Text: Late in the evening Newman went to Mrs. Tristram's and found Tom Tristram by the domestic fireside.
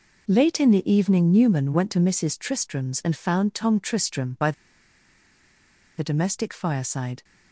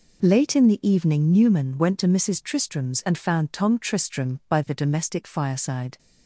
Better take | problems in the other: second | pauses between "by" and "the"; strong; at 4.5 s; 1.4 s long

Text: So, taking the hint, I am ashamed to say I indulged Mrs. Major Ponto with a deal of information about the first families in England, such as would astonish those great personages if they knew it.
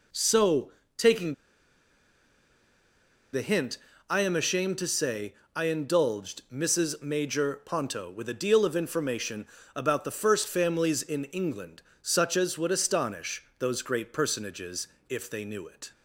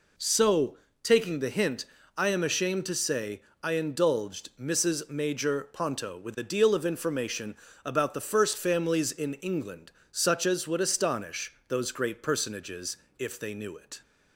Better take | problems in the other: second | pauses between "taking" and "the"; strong; at 1.3 s; 1.9 s long // pauses between "say" and "I"; slight; at 5.3 s; 0.20 s long; slight in the second // pauses between "information" and "about"; slight; at 9.4 s; 0.30 s long; slight in the second // pauses between "astonish" and "those"; slight; at 13.4 s; 0.16 s long; slight in the second // pauses between "personages" and "if"; slight; at 14.8 s; 0.20 s long; slight in the second

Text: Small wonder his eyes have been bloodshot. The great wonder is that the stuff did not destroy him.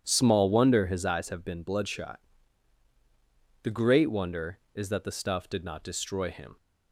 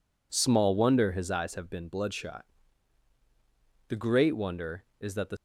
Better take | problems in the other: first | stops before "stuff did not destroy him"; at 5.3 s

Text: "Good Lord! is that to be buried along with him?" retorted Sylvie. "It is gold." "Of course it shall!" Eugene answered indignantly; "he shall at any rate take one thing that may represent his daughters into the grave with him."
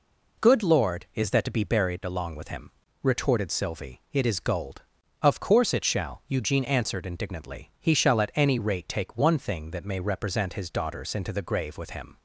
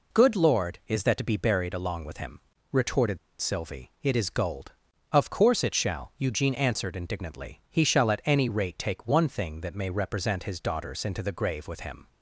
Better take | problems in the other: first | pauses between "retorted" and "Sylvie"; slight; at 3.1 s; 0.23 s long

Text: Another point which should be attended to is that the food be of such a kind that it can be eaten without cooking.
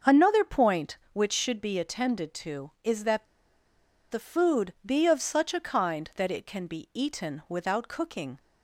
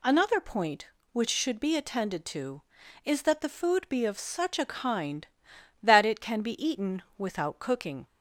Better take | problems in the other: second | starts louder than the rest; until 1.2 s; 6 dB // pauses between "that" and "the"; noticeable; at 3.2 s; 0.85 s long

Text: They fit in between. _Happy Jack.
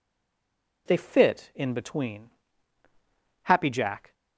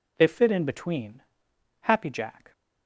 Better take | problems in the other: second | stays silent before the first word; slight; until 0.8 s; 0.8 s long

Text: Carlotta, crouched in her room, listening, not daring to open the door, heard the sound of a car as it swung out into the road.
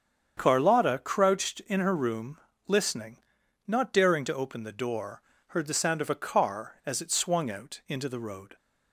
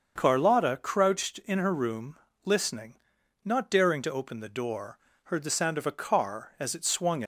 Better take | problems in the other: first | starts louder than the rest; until 1.1 s; 6.5 dB; strong in the first // stops before "out into the road"; at 7.2 s

